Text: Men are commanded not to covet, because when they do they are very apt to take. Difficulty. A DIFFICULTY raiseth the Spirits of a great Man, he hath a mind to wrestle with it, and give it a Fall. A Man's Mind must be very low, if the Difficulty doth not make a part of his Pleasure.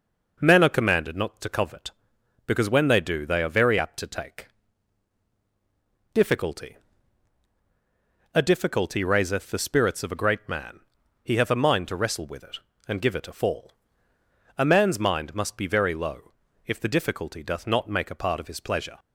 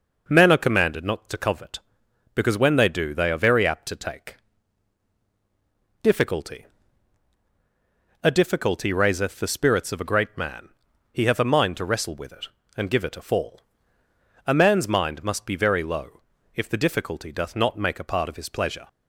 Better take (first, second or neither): neither